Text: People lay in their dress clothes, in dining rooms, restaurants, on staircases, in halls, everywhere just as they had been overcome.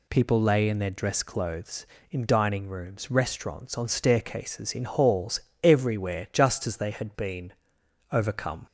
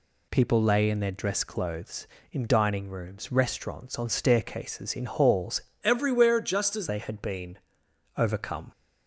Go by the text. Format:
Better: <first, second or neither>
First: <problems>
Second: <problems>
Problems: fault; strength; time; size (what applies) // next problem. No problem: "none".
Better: first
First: pauses between "been" and "overcome"; noticeable; at 7.5 s; 0.60 s long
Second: changes voice from "everywhere" to "as"; from 5.8 to 6.8 s; 1.0 s long // pauses between "been" and "overcome"; noticeable; at 7.5 s; 0.60 s long